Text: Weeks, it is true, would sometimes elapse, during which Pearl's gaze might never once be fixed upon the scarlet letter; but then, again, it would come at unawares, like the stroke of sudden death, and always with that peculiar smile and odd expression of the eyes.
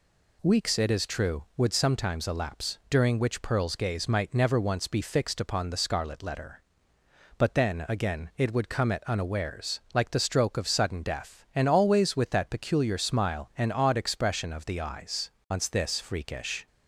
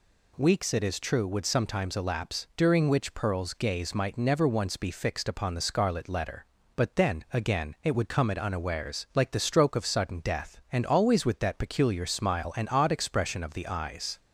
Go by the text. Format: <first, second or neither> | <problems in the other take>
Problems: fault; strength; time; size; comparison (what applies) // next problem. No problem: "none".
second | goes on to say "Once this freakish"; noticeable; from 15.5 s on; 1.1 s long